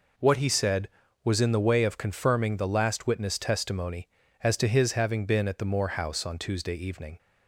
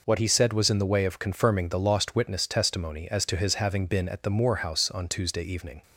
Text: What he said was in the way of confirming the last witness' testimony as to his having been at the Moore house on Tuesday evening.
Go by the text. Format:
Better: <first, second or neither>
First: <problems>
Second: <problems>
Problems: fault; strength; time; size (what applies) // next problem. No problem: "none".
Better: first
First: none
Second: says "lost" for "last"; at 1.7 s